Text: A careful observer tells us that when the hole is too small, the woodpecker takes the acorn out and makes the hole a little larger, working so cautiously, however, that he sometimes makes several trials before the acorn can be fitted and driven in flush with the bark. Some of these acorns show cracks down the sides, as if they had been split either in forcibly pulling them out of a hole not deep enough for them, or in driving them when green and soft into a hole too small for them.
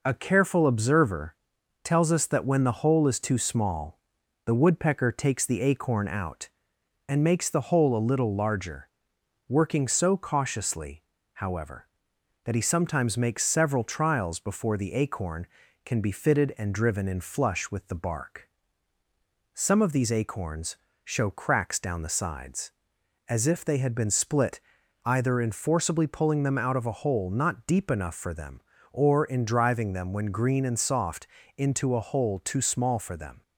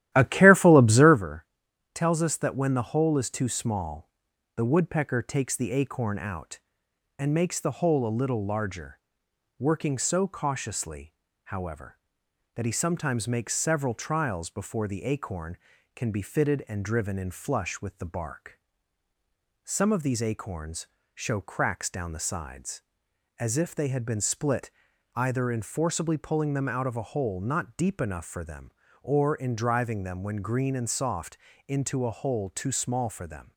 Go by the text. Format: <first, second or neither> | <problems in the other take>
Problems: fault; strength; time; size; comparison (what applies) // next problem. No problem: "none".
first | starts louder than the rest; strong; until 1.2 s; 13.5 dB // pauses between "observer" and "tells"; noticeable; at 1.4 s; 0.48 s long; noticeable in the first // pauses between "acorns" and "show"; slight; at 20.8 s; 0.26 s long; slight in the first // pauses between "split" and "either"; noticeable; at 24.6 s; 0.46 s long; noticeable in the first // pauses between "soft" and "into"; slight; at 31.3 s; 0.30 s long; slight in the first